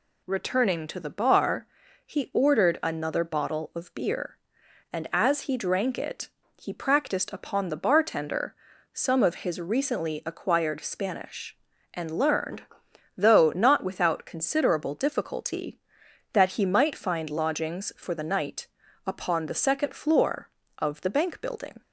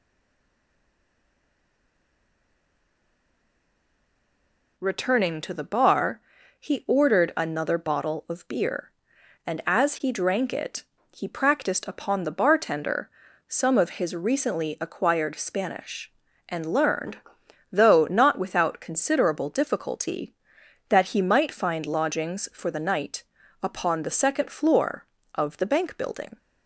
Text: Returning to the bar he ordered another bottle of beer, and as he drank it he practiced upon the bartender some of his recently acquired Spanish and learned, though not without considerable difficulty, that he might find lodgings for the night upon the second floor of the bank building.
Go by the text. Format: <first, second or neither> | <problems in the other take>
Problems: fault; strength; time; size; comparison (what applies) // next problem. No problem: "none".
first | stays silent before the first word; strong; until 4.7 s; 4.7 s long // pauses between "bar" and "he"; at 6.2 s; 0.38 s long; also in the first // pauses between "it" and "he"; slight; at 10.8 s; 0.32 s long; slight in the first // pauses between "bartender" and "some"; at 13.0 s; 0.38 s long; also in the first // pauses between "night" and "upon"; at 23.2 s; 0.38 s long; also in the first